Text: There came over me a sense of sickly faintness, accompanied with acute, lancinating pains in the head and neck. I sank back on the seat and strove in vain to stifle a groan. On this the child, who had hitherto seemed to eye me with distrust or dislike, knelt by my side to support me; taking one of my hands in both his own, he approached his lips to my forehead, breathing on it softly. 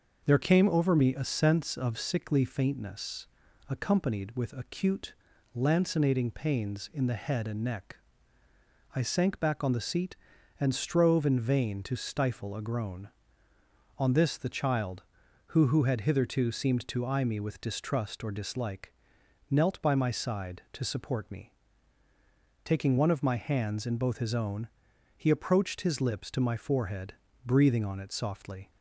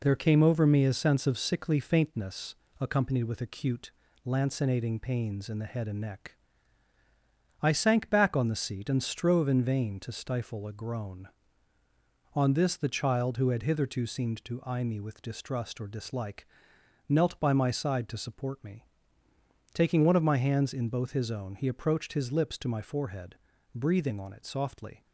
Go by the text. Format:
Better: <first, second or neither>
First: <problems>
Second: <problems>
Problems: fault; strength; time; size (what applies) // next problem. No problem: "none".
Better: second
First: starts louder than the rest; until 1.2 s; 6 dB // says "who" twice; at 15.6 s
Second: none